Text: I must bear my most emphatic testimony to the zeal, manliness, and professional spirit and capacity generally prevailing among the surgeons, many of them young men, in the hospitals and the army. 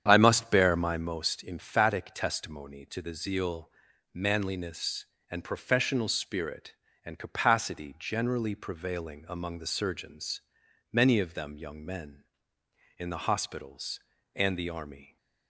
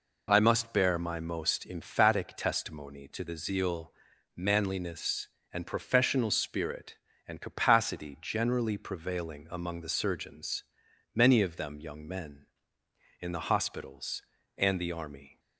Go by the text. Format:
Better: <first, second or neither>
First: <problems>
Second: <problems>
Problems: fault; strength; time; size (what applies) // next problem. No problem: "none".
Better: second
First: starts louder than the rest; strong; until 1.2 s; 8.5 dB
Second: none